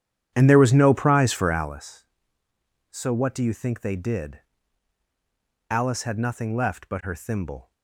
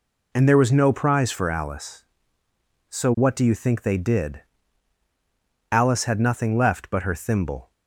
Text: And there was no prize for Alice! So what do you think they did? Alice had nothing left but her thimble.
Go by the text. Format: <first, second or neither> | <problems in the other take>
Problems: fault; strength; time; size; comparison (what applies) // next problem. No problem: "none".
second | starts louder than the rest; strong; until 1.8 s; 10 dB